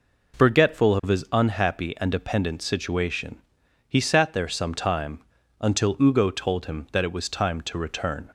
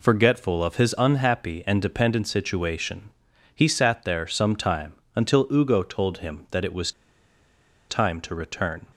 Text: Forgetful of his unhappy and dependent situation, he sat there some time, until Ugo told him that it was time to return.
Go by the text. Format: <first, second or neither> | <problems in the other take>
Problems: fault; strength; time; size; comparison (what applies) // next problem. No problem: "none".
first | pauses between "was" and "time"; at 6.9 s; 0.98 s long